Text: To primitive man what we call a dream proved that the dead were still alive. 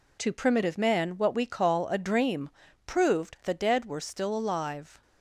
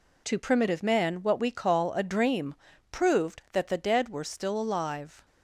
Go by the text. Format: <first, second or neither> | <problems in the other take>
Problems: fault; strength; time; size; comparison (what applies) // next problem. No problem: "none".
second | pauses between "dream" and "proved"; at 2.4 s; 0.38 s long; also in the second // skips "that"; at 3.4 s